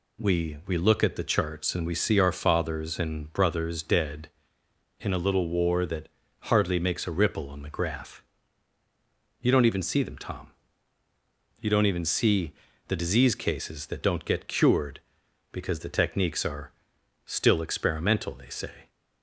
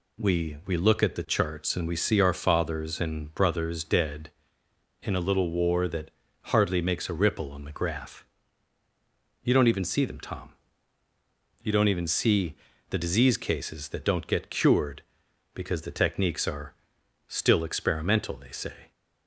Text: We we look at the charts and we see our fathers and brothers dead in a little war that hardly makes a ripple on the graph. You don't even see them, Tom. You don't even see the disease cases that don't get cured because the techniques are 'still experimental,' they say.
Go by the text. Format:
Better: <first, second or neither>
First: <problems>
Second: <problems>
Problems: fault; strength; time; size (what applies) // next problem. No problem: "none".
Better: neither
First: pauses between "that" and "hardly"; slight; at 6.0 s; 0.32 s long // pauses between "see" and "the"; at 12.5 s; 0.38 s long // pauses between "are" and "still"; noticeable; at 16.7 s; 0.52 s long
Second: pauses between "that" and "hardly"; slight; at 6.1 s; 0.32 s long // pauses between "see" and "the"; at 12.5 s; 0.38 s long // pauses between "are" and "still"; noticeable; at 16.7 s; 0.52 s long